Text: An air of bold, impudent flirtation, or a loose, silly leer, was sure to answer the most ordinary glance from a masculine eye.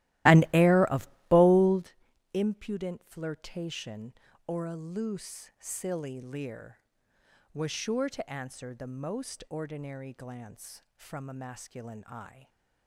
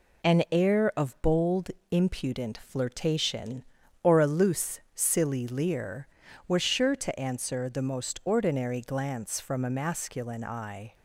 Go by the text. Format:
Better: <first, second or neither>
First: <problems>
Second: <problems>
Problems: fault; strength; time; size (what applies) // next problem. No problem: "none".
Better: second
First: starts louder than the rest; strong; until 1.9 s; 16.5 dB // pauses between "of" and "bold"; slight; at 1.0 s; 0.22 s long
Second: none